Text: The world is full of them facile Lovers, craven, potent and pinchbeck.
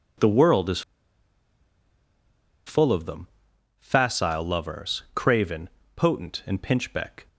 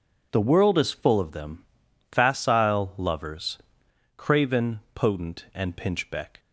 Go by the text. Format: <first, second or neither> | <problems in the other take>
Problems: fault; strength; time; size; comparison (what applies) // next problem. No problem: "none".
second | pauses between "is" and "full"; strong; at 0.8 s; 1.8 s long // pauses between "them" and "facile"; noticeable; at 3.2 s; 0.50 s long; noticeable in the second